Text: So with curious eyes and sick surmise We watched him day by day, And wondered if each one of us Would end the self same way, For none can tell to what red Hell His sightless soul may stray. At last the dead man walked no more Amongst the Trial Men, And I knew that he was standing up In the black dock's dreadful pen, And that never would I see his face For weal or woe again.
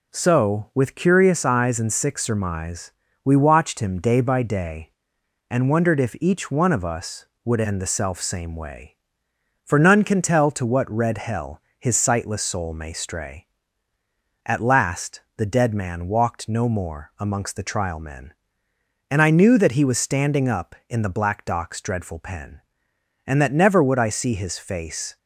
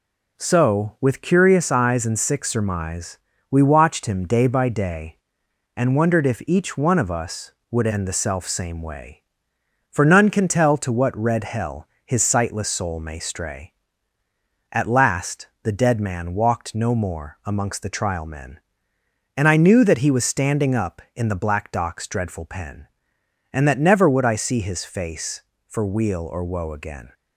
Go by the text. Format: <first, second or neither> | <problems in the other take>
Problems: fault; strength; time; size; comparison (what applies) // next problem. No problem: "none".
second | pauses between "surmise" and "We"; slight; at 2.9 s; 0.32 s long; slight in the second // pauses between "Hell" and "His"; slight; at 11.6 s; 0.18 s long; slight in the second // pauses between "last" and "the"; slight; at 15.2 s; 0.16 s long; slight in the second // stops before "For weal or woe again"; at 25.1 s